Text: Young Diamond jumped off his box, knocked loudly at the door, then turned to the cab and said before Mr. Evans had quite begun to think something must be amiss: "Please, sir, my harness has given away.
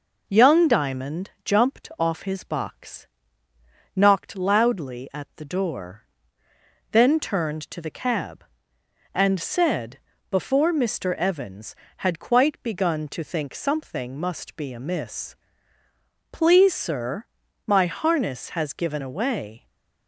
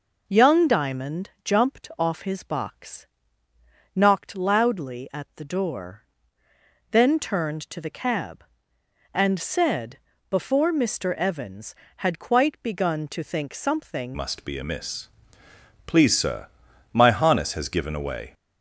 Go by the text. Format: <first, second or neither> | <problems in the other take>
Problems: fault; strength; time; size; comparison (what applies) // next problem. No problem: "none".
first | pauses between "said" and "before"; slight; at 9.9 s; 0.30 s long; slight in the first // changes voice at "must"; from 14.1 s on; 4.2 s long